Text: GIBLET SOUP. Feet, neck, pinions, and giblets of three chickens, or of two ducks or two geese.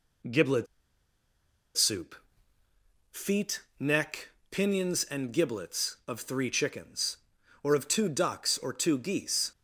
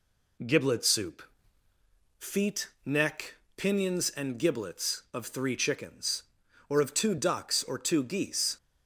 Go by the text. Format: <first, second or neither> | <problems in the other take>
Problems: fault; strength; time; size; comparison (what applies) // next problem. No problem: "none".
second | pauses between "GIBLET" and "SOUP"; at 0.6 s; 1.1 s long